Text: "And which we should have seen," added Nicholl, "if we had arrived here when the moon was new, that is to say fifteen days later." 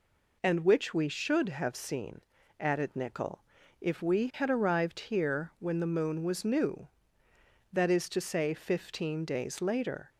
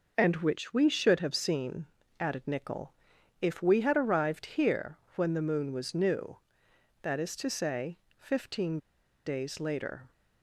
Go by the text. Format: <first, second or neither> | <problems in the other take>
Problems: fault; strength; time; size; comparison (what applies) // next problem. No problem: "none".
first | pauses between "here" and "when"; slight; at 4.9 s; 0.20 s long // pauses between "say" and "fifteen"; slight; at 7.9 s; 0.20 s long // pauses between "fifteen" and "days"; noticeable; at 8.7 s; 0.46 s long